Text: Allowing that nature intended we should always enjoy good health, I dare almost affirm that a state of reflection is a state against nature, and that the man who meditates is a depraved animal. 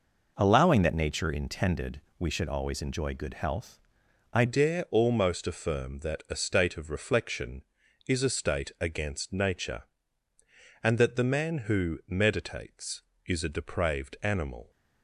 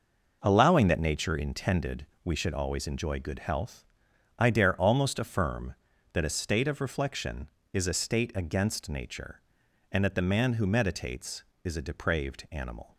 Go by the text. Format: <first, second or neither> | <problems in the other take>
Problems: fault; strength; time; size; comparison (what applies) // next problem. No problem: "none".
second | pauses between "intended" and "we"; slight; at 2.0 s; 0.18 s long; slight in the second // changes voice at "dare"; from 4.4 s on; 10.2 s long